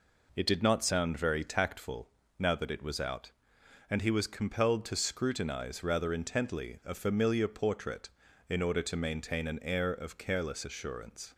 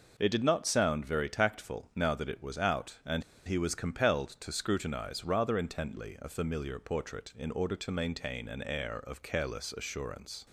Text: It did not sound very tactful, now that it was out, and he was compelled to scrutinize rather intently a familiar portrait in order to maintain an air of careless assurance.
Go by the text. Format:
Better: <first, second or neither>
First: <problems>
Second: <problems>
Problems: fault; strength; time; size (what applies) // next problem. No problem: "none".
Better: first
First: none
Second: pauses between "and" and "he"; slight; at 3.2 s; 0.24 s long